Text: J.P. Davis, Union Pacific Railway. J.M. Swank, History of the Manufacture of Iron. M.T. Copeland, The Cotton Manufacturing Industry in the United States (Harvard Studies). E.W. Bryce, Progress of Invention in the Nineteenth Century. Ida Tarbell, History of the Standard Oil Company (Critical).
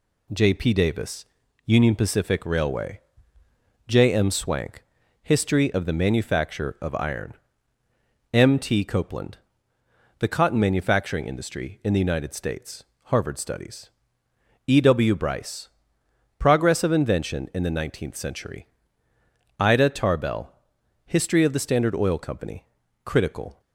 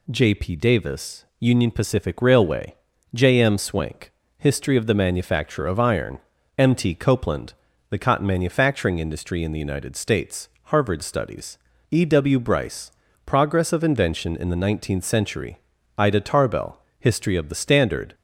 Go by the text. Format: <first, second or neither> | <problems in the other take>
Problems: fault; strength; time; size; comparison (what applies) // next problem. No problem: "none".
first | stops before "Oil Company Critical"; at 18.1 s